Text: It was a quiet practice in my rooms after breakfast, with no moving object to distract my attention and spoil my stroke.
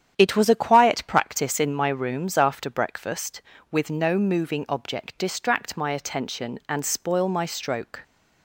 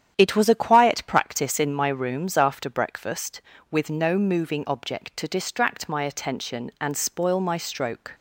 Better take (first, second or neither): second